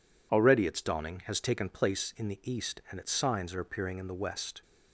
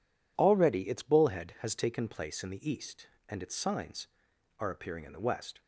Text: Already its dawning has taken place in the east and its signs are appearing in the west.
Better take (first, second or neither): first